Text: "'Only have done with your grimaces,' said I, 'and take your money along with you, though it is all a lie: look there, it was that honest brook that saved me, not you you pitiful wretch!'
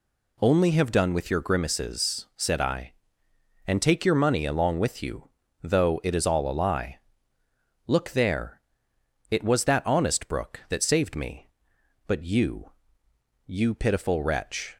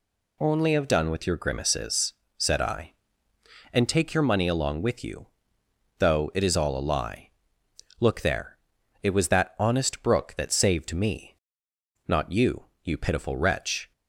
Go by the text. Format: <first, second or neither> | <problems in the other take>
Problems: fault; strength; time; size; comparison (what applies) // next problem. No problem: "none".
second | says "but" for "not"; at 12.0 s // pauses between "you" and "you"; noticeable; at 12.7 s; 0.76 s long; slight in the second